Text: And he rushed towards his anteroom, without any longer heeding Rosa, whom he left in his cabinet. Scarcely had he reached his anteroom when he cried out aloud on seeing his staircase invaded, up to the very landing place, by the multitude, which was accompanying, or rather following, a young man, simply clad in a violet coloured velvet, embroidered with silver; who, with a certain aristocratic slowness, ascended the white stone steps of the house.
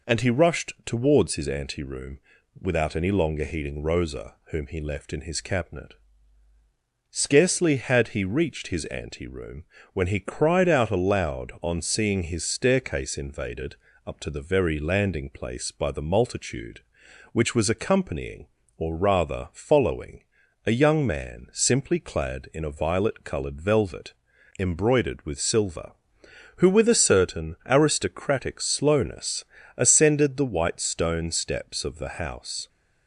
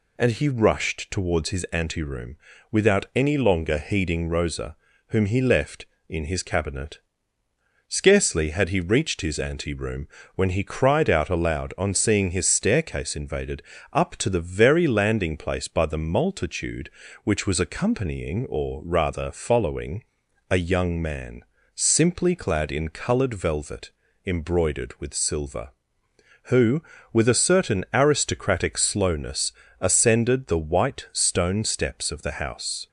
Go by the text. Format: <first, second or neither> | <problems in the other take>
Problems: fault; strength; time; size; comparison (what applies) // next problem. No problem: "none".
first | pauses between "anteroom" and "when"; slight; at 10.0 s; 0.28 s long; slight in the first // skips "a violet"; at 22.8 s